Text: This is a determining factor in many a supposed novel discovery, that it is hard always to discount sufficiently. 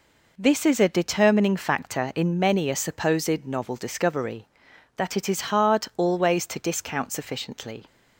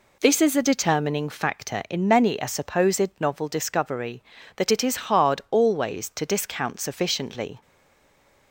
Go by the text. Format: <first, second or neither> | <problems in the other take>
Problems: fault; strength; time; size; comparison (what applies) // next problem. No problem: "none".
first | stays silent after the last word; slight; from 7.6 s on; 0.9 s long